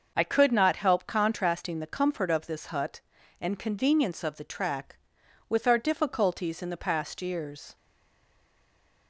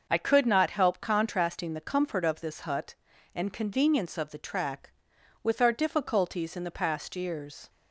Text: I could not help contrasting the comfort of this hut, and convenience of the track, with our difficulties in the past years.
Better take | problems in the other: second | starts louder than the rest; noticeable; until 1.1 s; 6 dB; noticeable in the second // stays silent after the last word; noticeable; from 7.7 s on; 1.3 s long

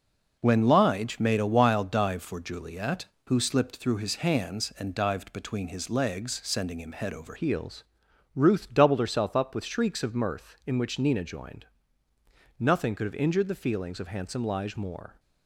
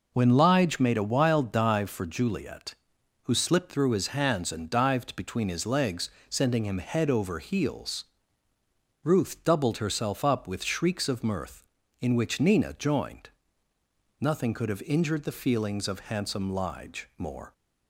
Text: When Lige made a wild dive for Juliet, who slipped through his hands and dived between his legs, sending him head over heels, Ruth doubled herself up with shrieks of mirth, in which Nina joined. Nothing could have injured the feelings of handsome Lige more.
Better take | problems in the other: second | changes voice at "heels"; from 7.3 s on; 7.8 s long

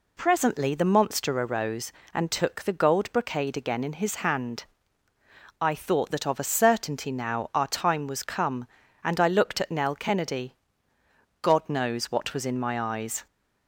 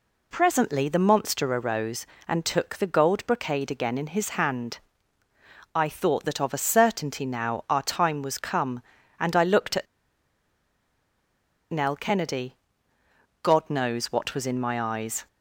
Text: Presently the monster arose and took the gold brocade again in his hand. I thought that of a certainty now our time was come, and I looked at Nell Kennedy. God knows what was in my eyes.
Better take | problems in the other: first | pauses between "at" and "Nell"; strong; at 9.8 s; 1.8 s long

